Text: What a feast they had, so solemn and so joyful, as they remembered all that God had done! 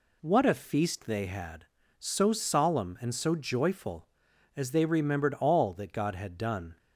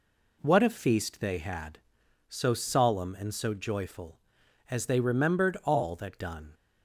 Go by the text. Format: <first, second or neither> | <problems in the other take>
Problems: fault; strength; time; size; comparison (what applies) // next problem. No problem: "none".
first | skips "God had"; at 6.2 s